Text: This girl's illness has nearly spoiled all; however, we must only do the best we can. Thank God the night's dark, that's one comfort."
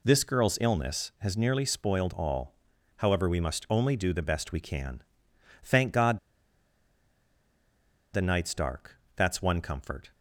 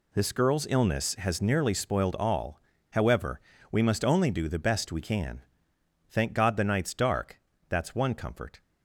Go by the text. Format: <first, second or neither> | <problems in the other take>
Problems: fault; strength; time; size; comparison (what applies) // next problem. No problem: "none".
second | pauses between "God" and "the"; strong; at 6.1 s; 1.9 s long